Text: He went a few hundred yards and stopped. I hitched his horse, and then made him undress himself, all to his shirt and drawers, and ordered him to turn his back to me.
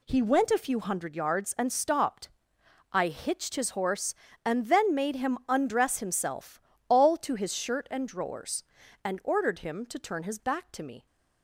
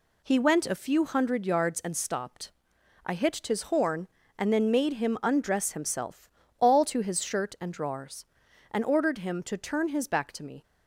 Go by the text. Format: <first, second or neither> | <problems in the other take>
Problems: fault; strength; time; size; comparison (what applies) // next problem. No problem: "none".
first | says "horn" for "horse"; at 3.6 s